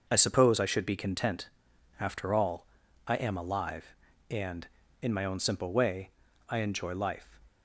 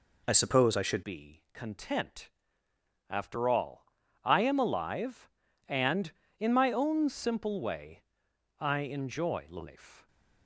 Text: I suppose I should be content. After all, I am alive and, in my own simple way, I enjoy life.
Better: first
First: none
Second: changes voice at "be"; from 1.0 s on; 9.0 s long

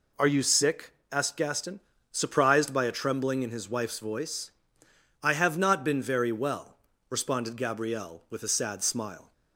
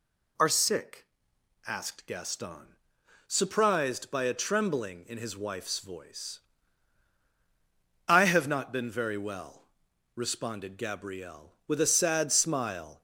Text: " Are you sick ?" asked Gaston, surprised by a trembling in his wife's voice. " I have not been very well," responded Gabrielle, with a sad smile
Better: first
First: none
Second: skips "you"; at 0.5 s

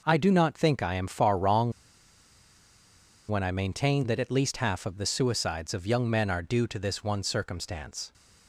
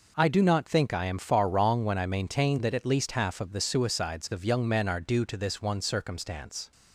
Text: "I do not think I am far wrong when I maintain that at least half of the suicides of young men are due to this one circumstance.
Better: second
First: pauses between "wrong" and "when"; strong; at 1.7 s; 1.5 s long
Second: none

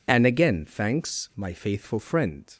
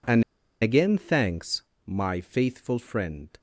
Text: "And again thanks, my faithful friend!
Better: first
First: none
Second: pauses between "And" and "again"; at 0.2 s; 0.39 s long

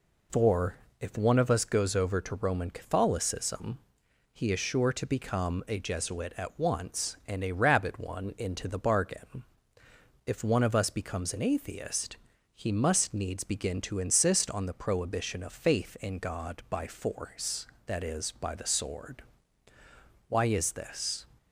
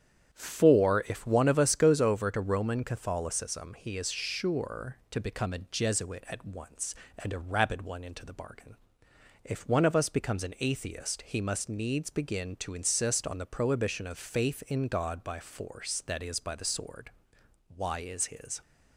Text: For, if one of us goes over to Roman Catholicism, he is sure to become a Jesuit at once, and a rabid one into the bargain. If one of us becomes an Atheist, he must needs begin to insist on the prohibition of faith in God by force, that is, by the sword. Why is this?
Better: first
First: none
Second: starts louder than the rest; strong; until 1.3 s; 9 dB // says "his" for "this"; at 18.2 s

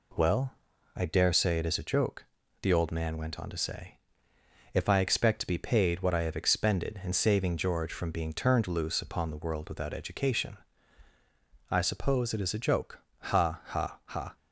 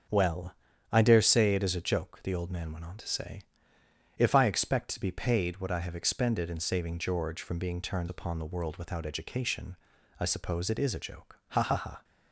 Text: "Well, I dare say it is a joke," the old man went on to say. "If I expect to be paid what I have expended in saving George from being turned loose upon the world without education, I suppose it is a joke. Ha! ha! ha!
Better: first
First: none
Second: starts louder than the rest; until 1.4 s; 6.5 dB // skips "loose"; at 8.0 s

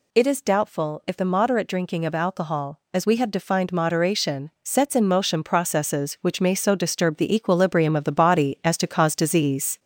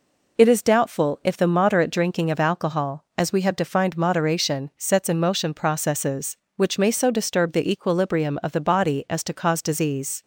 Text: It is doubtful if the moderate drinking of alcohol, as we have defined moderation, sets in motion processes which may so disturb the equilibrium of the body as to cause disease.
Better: second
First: gets louder; throughout; 4 dB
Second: none

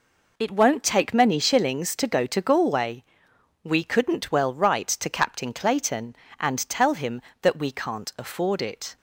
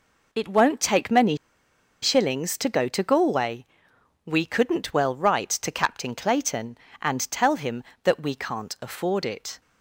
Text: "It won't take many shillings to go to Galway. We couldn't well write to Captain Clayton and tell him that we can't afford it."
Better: first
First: none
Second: pauses between "many" and "shillings"; noticeable; at 1.3 s; 0.66 s long

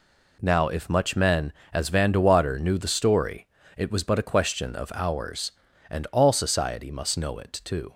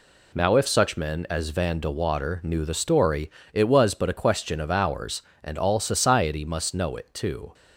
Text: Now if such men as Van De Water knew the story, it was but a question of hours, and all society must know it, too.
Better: second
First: says "much" for "such"; at 0.8 s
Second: none

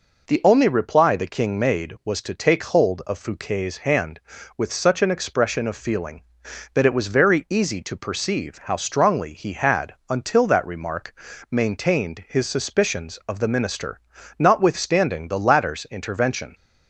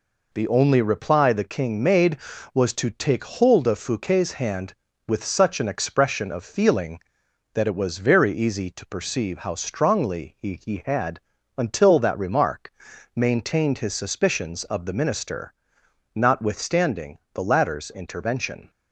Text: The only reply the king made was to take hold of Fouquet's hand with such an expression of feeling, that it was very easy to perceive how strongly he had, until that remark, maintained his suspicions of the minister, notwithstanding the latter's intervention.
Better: first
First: none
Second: says "he" twice; at 10.6 s // pauses between "notwithstanding" and "the"; slight; at 17.1 s; 0.16 s long

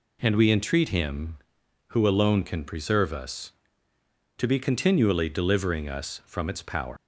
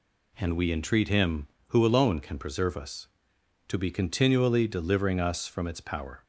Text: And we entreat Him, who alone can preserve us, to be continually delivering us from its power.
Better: second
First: leaves "power" unfinished; at 6.9 s; 135 ms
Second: none

